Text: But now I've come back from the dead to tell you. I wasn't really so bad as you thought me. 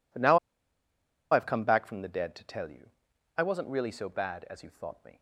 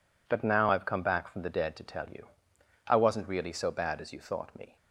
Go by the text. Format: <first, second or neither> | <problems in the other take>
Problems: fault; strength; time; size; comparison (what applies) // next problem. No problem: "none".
second | pauses between "now" and "I've"; noticeable; at 0.3 s; 0.93 s long